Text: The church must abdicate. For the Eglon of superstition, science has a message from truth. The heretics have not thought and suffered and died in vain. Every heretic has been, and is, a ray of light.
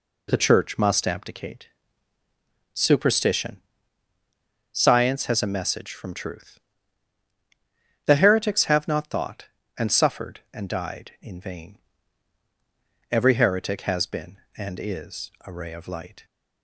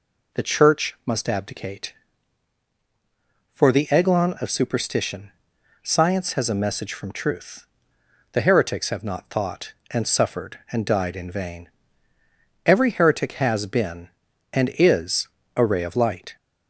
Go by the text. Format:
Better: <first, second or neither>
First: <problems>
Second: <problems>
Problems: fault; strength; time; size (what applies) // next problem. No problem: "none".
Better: second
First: skips "For the Eglon of"; at 2.2 s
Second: none